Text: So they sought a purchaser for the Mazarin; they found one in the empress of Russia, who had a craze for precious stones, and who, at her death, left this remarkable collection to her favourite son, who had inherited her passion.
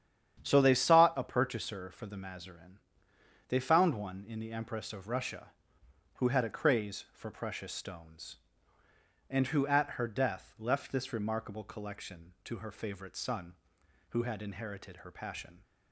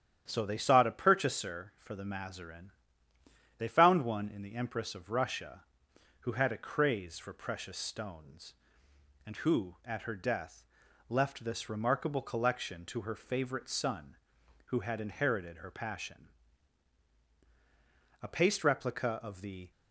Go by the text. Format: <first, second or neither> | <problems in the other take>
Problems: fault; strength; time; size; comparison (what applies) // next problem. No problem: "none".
first | starts louder than the rest; strong; until 1.2 s; 10 dB; strong in the first // goes on to say "A paste replica of the"; from 18.2 s on; 1.5 s long